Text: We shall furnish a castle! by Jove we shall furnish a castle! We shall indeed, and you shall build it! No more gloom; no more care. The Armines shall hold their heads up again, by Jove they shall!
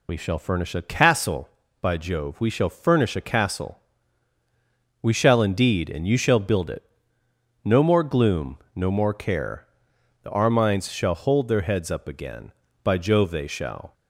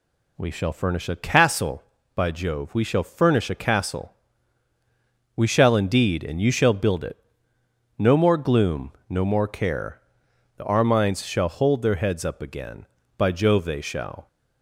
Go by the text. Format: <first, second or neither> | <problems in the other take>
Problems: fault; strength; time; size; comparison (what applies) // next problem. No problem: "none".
second | loses the start of "We"; at 0.0 s; 55 ms